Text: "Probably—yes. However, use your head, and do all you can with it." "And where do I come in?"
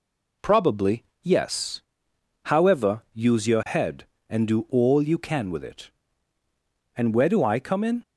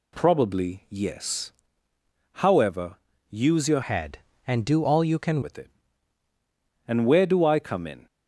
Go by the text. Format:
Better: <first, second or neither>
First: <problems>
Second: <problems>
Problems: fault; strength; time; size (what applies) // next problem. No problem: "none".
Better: first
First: none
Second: changes voice from "head" to "can"; from 3.8 to 5.4 s; 1.6 s long